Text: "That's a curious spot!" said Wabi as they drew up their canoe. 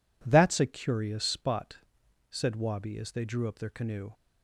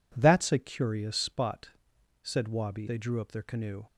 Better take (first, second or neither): first